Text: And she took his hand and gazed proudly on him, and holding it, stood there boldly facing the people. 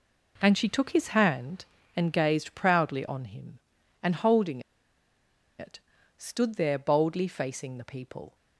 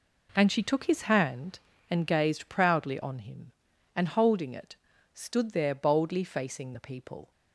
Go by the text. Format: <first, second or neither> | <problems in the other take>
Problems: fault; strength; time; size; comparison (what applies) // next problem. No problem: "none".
second | pauses between "holding" and "it"; at 4.6 s; 0.98 s long